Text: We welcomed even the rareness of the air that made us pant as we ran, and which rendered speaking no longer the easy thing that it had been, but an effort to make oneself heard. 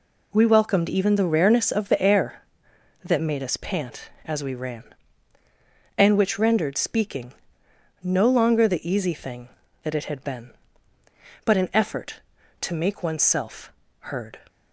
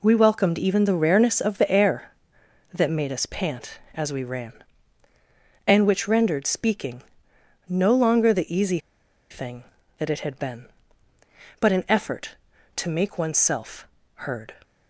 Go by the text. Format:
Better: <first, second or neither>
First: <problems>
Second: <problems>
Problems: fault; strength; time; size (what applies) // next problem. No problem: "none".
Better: first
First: pauses between "speaking" and "no"; noticeable; at 7.3 s; 0.69 s long // pauses between "oneself" and "heard"; at 13.7 s; 0.40 s long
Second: pauses between "speaking" and "no"; noticeable; at 7.0 s; 0.66 s long // pauses between "easy" and "thing"; noticeable; at 8.7 s; 0.52 s long // pauses between "oneself" and "heard"; at 13.8 s; 0.40 s long